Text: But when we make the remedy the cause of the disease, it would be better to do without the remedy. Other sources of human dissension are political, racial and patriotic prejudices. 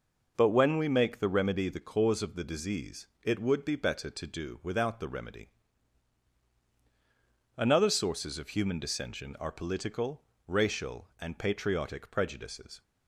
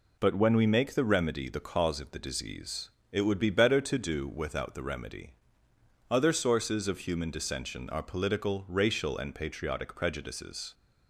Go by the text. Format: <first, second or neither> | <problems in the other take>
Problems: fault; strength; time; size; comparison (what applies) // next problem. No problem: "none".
second | says "Another" for "Other"; at 7.5 s